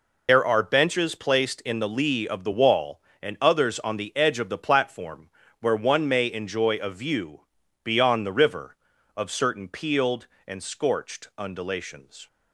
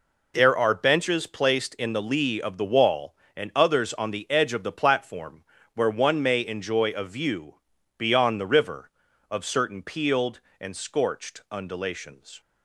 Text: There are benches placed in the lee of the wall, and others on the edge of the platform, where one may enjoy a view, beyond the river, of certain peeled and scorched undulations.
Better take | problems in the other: second | loses the start of "There"; at 0.2 s; 65 ms

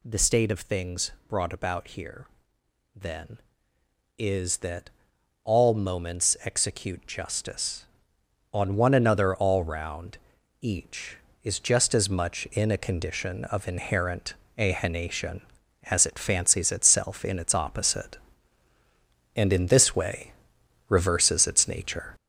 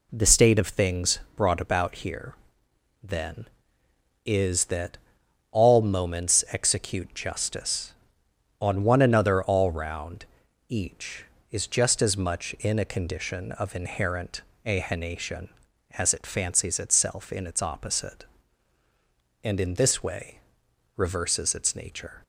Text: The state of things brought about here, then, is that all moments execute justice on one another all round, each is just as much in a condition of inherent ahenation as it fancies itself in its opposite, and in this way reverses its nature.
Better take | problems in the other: second | gets louder; noticeable; throughout; 5.5 dB // pauses between "things" and "brought"; slight; at 1.1 s; 0.16 s long; slight in the second // pauses between "that" and "all"; noticeable; at 4.8 s; 0.56 s long; noticeable in the second // pauses between "inherent" and "ahenation"; slight; at 14.3 s; 0.24 s long; slight in the second // pauses between "way" and "reverses"; noticeable; at 20.3 s; 0.56 s long; noticeable in the second

